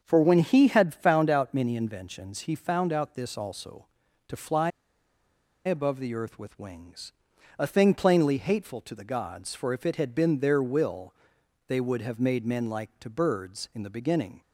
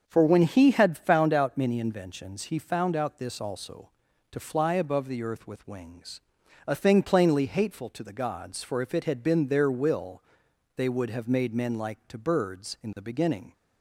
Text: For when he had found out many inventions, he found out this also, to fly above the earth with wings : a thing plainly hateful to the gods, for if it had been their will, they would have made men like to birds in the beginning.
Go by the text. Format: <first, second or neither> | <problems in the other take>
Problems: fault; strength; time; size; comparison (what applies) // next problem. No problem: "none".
second | starts louder than the rest; until 1.0 s; 6.5 dB; also in the second // pauses between "fly" and "above"; noticeable; at 4.6 s; 0.95 s long